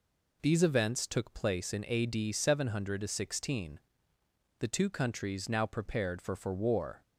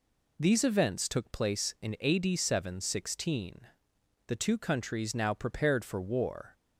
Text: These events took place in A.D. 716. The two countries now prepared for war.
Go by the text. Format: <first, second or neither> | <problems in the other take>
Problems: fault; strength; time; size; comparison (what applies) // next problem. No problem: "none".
second | says "for" twice; at 6.3 s